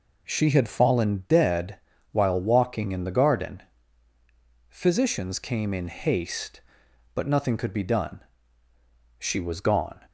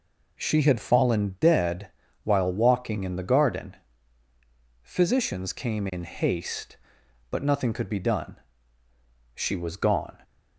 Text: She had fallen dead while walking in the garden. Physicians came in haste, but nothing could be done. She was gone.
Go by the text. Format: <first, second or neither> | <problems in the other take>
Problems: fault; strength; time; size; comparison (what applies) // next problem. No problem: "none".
neither | pauses between "dead" and "while"; slight; the same in both